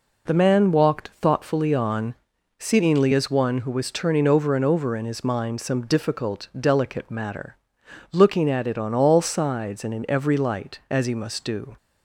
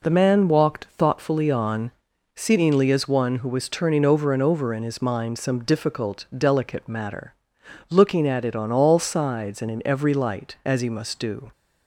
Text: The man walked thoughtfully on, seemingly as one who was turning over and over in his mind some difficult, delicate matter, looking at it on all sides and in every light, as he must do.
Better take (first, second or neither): neither